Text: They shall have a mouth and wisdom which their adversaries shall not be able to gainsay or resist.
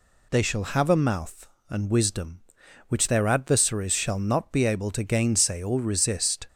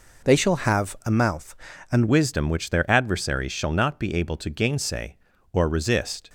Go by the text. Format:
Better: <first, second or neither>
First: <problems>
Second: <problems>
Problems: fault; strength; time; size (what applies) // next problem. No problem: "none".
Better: first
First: none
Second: changes voice at "wisdom"; from 2.0 s on; 4.2 s long